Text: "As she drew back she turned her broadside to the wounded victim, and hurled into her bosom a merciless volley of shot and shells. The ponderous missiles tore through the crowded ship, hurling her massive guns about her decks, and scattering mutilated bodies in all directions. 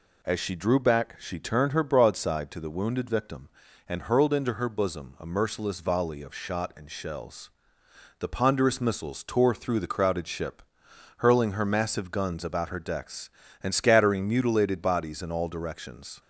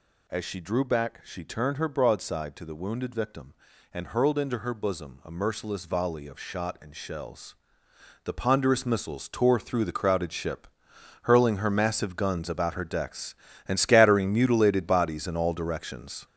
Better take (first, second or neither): first